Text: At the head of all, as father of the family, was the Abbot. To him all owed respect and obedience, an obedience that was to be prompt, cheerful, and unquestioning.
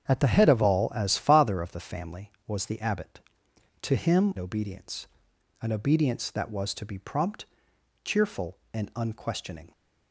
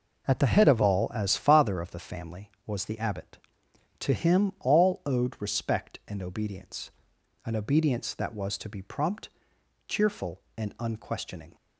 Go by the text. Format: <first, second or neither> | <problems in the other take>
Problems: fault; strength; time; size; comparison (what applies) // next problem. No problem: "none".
second | starts louder than the rest; strong; until 1.1 s; 8 dB // skips "all owed respect and"; at 4.3 s